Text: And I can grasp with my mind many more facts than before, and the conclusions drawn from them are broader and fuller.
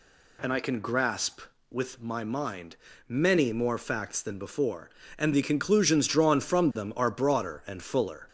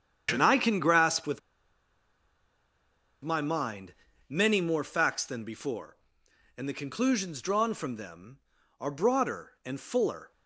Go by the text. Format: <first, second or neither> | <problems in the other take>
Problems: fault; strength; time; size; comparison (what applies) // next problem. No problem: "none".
first | starts louder than the rest; strong; until 1.3 s; 8.5 dB // pauses between "with" and "my"; strong; at 1.3 s; 1.8 s long // pauses between "mind" and "many"; slight; at 3.9 s; 0.34 s long; slight in the first